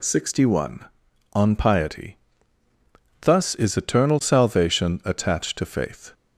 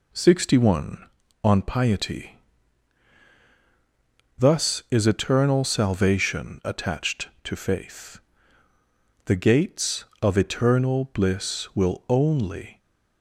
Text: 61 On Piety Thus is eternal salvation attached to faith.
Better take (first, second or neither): first